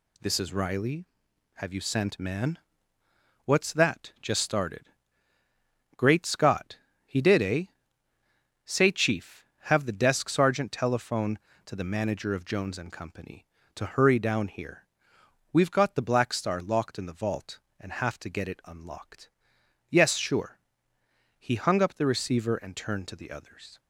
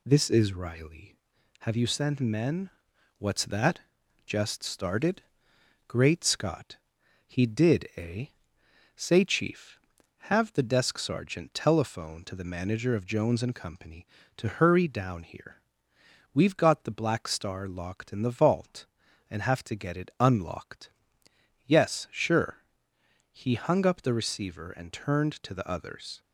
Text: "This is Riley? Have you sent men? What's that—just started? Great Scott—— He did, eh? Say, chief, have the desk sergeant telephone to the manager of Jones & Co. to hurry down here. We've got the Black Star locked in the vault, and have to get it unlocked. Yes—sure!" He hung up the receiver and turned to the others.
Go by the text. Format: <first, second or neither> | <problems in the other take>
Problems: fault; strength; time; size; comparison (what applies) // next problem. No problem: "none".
second | says "man" for "men"; at 2.1 s